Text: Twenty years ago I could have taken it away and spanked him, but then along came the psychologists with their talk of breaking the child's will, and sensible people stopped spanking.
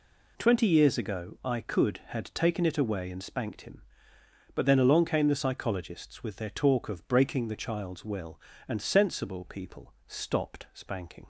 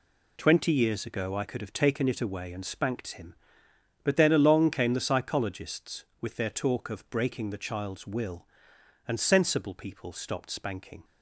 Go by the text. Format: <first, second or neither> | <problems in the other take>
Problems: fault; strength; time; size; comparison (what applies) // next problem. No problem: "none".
second | says "had" for "have"; at 2.0 s